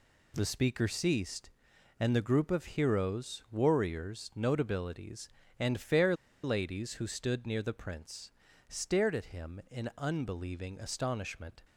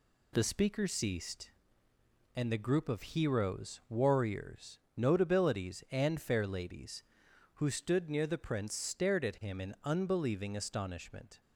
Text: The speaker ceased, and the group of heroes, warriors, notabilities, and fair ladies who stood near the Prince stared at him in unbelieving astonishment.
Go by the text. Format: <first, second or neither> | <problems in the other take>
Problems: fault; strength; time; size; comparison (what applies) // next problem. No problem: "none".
second | pauses between "fair" and "ladies"; slight; at 6.1 s; 0.30 s long // pauses between "Prince" and "stared"; at 8.3 s; 0.38 s long